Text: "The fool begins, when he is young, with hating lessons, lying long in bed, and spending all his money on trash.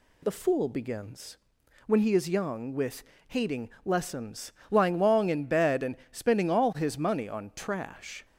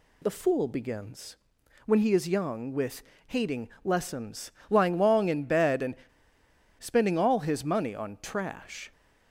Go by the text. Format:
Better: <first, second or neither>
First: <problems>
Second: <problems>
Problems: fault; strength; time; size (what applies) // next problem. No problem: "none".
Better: first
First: pauses between "with" and "hating"; slight; at 3.0 s; 0.24 s long // pauses between "hating" and "lessons"; slight; at 3.6 s; 0.16 s long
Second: pauses between "with" and "hating"; slight; at 3.0 s; 0.24 s long // pauses between "hating" and "lessons"; slight; at 3.6 s; 0.16 s long // pauses between "and" and "spending"; noticeable; at 5.9 s; 0.82 s long